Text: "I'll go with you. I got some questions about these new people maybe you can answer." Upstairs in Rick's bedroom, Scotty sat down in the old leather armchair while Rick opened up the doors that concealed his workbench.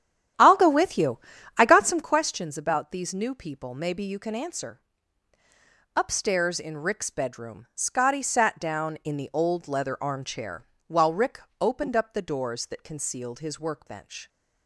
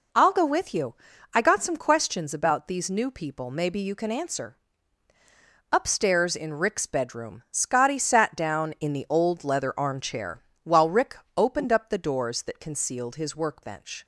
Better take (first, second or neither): second